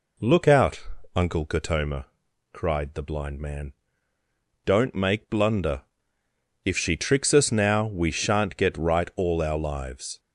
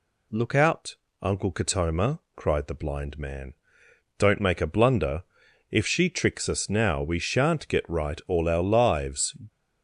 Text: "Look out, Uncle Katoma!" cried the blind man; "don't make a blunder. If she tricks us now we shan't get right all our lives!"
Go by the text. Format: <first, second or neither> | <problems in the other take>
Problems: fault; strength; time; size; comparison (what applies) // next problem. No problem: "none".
second | skips "a"; at 5.2 s